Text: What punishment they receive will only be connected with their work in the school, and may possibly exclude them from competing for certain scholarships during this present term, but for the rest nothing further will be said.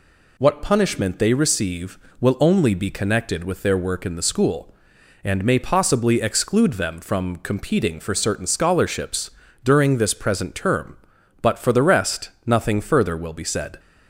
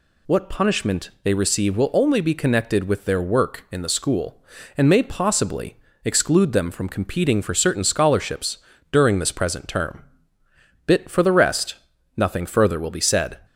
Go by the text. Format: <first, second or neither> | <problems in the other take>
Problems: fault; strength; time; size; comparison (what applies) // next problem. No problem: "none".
first | pauses between "possibly" and "exclude"; slight; at 5.7 s; 0.28 s long // pauses between "scholarships" and "during"; slight; at 8.5 s; 0.34 s long; slight in the first // says "bit" for "but"; at 10.8 s // pauses between "rest" and "nothing"; at 11.7 s; 0.42 s long; slight in the first